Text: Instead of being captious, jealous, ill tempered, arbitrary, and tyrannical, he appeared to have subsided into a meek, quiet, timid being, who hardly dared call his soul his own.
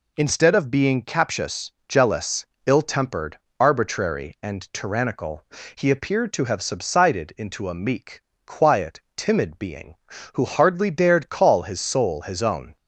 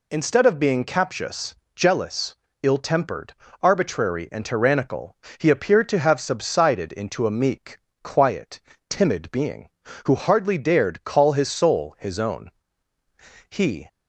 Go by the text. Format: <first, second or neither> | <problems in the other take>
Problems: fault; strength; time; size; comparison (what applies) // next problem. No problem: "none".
first | goes on to say "He"; slight; from 13.4 s on; 0.38 s long